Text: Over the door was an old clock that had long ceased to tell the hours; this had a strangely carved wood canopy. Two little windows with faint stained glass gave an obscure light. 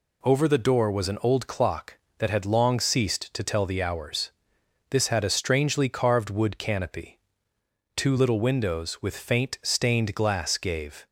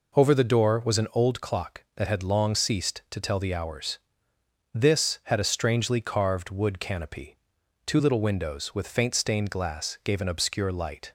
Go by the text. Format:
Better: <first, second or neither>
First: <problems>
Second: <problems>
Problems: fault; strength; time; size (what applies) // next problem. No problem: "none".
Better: second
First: stops before "an obscure light"; at 11.0 s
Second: none